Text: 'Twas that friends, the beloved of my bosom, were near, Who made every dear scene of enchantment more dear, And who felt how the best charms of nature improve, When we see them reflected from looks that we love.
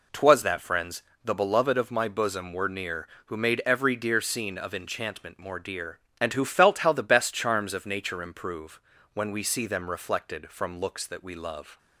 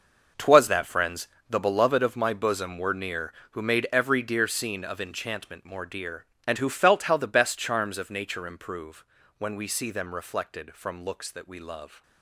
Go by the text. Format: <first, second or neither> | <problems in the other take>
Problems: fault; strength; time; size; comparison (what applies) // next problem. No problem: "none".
first | gets quieter; strong; throughout; 13 dB